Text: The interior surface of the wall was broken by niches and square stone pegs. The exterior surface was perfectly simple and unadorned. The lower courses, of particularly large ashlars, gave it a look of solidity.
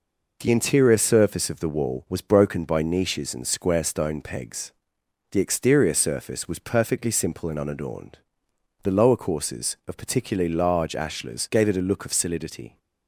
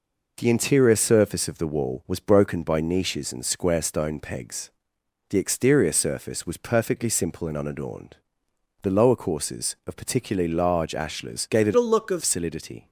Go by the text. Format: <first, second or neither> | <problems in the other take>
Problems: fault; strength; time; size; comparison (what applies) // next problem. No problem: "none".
first | changes voice from "a" to "of"; from 11.7 to 12.2 s; 0.5 s long